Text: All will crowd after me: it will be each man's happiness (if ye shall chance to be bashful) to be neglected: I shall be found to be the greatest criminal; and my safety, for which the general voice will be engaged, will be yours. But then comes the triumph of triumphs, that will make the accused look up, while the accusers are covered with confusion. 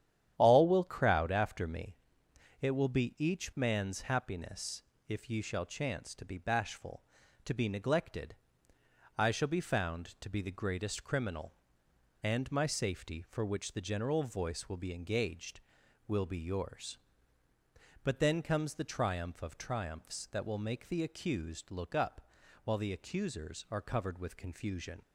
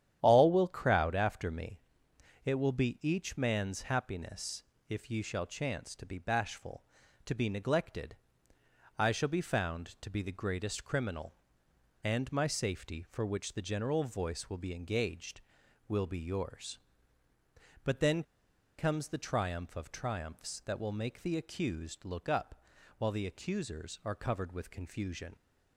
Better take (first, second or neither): first